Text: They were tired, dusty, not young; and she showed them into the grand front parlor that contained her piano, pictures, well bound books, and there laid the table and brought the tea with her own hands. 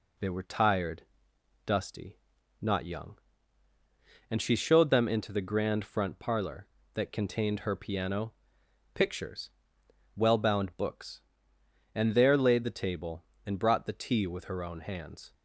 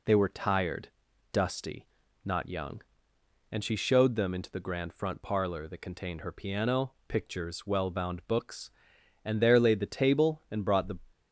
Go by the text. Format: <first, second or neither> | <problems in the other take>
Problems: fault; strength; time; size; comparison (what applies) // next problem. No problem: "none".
first | stops before "tea with her own hands"; at 11.1 s